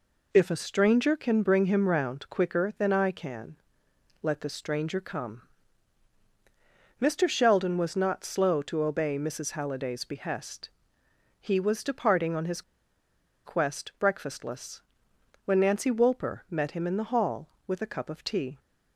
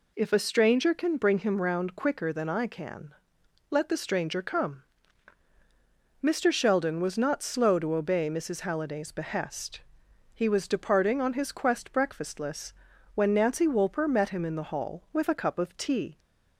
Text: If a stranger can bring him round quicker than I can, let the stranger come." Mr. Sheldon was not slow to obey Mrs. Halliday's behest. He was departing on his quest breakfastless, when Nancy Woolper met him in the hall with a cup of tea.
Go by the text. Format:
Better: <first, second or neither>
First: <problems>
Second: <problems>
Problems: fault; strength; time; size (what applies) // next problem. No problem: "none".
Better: second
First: pauses between "his" and "quest"; noticeable; at 12.6 s; 0.84 s long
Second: none